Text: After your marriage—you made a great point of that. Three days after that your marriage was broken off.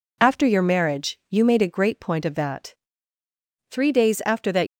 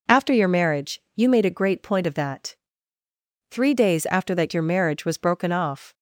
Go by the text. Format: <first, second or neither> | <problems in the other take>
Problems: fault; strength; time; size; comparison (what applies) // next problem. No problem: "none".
second | stops before "your marriage was broken off"; at 4.6 s